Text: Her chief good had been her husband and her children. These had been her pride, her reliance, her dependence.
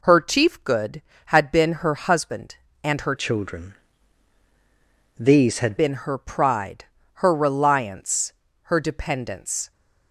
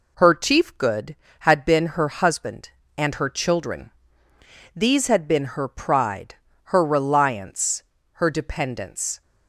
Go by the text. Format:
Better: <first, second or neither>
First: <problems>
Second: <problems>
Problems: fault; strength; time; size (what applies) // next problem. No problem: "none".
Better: second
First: changes voice from "children" to "had"; from 3.1 to 5.7 s; 2.6 s long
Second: none